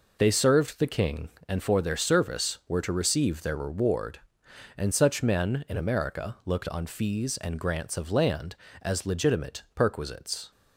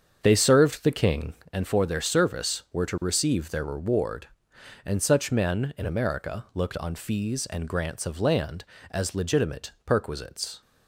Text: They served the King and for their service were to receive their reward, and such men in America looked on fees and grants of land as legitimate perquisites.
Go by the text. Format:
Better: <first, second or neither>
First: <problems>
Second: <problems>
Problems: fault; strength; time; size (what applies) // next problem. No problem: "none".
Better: first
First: none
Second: starts louder than the rest; strong; until 1.5 s; 7 dB